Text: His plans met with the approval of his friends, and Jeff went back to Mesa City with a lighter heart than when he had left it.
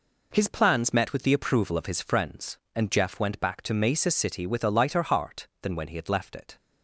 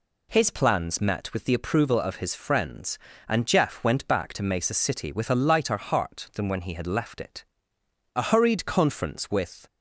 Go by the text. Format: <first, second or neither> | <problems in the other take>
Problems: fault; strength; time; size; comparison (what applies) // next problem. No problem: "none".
first | goes on to say "A hurried conference with"; from 8.1 s on; 1.5 s long